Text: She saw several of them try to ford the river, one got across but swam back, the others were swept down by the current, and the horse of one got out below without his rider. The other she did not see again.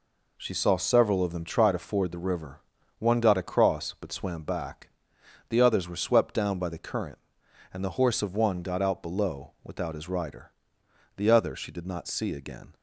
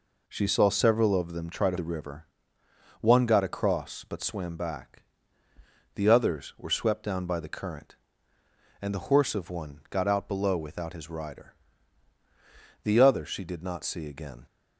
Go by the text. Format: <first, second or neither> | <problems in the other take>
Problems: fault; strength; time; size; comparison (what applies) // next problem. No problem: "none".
first | skips "ford"; at 1.7 s